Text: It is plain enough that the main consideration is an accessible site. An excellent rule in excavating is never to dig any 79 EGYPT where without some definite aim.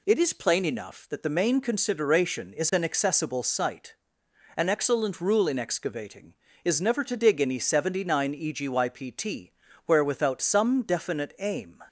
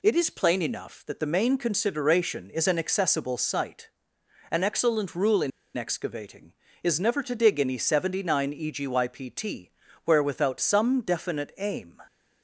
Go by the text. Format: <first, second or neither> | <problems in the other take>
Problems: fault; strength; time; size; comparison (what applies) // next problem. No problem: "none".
first | pauses between "in" and "excavating"; slight; at 5.5 s; 0.26 s long // pauses between "EGYPT" and "where"; slight; at 9.6 s; 0.36 s long; slight in the first